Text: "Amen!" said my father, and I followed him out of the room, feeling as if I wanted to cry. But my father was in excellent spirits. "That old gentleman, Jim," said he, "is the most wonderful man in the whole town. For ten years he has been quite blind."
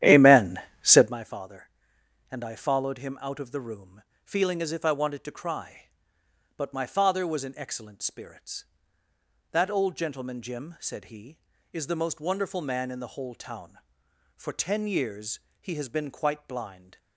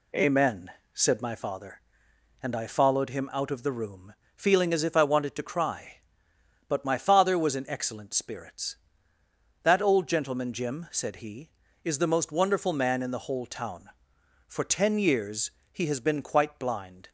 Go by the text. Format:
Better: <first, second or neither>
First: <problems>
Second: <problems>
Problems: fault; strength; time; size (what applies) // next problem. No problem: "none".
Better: second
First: starts louder than the rest; strong; until 1.2 s; 11.5 dB // pauses between "years" and "he"; slight; at 15.3 s; 0.22 s long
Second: pauses between "years" and "he"; slight; at 15.4 s; 0.22 s long